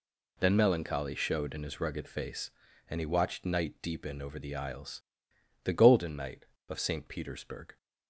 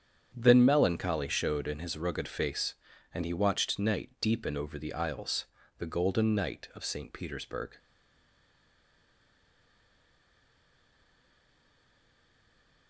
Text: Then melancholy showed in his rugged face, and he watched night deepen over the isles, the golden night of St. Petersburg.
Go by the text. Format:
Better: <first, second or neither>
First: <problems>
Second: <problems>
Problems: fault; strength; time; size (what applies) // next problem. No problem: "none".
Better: first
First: none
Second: starts louder than the rest; strong; until 1.3 s; 8 dB // stays silent after the last word; strong; from 7.7 s on; 5.1 s long